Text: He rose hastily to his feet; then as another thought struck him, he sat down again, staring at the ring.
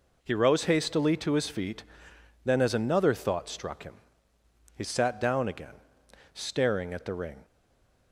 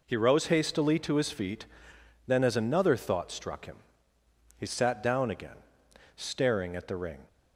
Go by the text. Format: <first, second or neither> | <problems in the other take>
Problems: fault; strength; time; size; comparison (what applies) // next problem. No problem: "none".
second | stays silent after the last word; slight; from 7.4 s on; 0.7 s long